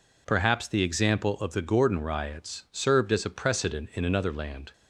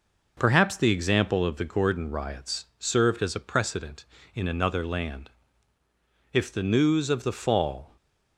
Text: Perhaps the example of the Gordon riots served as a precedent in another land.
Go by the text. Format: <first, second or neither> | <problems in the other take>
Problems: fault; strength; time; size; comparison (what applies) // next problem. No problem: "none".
first | goes on to say "If the news of the fall"; from 6.3 s on; 1.6 s long